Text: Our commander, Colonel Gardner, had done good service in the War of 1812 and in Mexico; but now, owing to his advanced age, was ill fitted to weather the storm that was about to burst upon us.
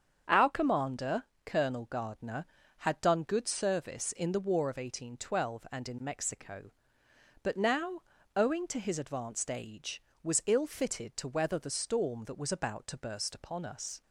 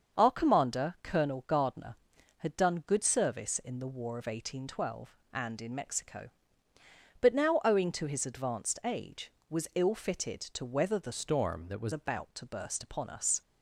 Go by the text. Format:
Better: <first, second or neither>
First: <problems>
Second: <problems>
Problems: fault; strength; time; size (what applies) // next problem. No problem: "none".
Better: first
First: starts louder than the rest; strong; until 1.4 s; 7.5 dB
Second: starts louder than the rest; until 1.2 s; 7 dB // changes voice from "storm" to "was"; from 11.1 to 11.9 s; 0.8 s long